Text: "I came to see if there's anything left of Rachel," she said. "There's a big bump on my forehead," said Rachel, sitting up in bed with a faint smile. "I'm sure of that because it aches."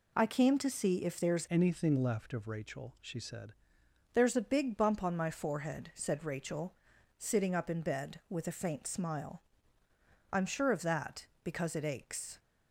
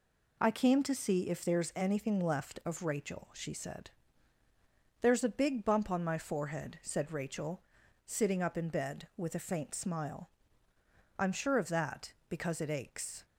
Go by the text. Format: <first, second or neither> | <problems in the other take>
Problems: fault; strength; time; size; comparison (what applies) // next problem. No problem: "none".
second | changes voice from "anything" to "said"; from 1.4 to 3.5 s; 2.1 s long